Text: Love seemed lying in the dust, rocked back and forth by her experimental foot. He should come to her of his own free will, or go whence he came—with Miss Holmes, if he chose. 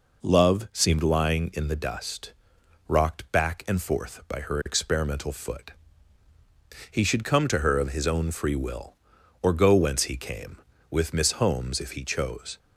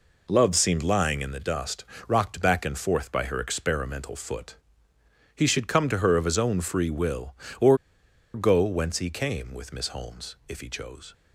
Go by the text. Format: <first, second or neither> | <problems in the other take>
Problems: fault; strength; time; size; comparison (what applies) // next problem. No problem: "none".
first | pauses between "or" and "go"; noticeable; at 7.7 s; 0.57 s long